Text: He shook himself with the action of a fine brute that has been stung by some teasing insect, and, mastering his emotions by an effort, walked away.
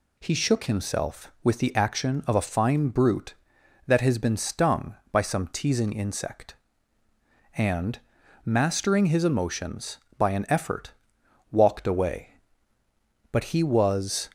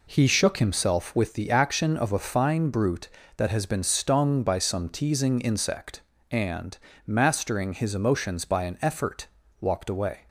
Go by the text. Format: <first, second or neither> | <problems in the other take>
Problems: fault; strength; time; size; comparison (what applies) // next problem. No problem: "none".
second | goes on to say "But he was"; noticeable; from 13.3 s on; 0.98 s long